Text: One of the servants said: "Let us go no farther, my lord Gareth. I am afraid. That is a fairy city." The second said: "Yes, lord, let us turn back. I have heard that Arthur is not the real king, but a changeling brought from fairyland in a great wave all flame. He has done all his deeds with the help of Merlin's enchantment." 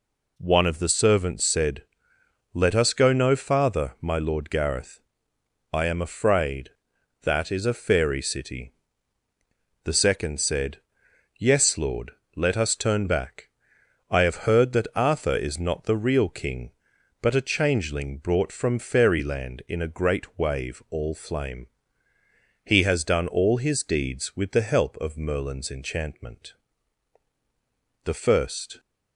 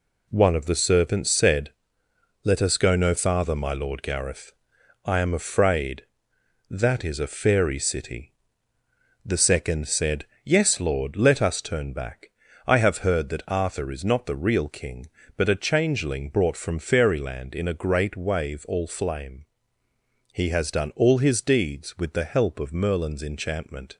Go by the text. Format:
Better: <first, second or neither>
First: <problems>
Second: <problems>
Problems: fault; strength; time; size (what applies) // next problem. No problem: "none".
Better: second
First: goes on to say "The first"; noticeable; from 28.0 s on; 0.76 s long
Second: none